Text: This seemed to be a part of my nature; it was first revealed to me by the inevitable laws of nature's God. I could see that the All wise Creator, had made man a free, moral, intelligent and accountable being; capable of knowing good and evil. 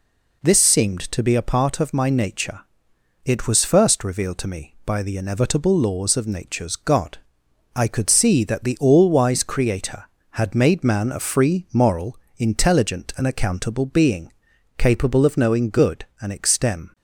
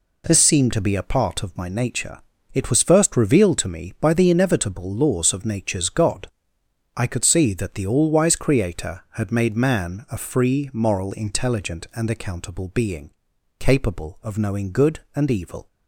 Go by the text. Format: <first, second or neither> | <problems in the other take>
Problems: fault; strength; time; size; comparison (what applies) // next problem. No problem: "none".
second | says "extem" for "evil"; at 16.3 s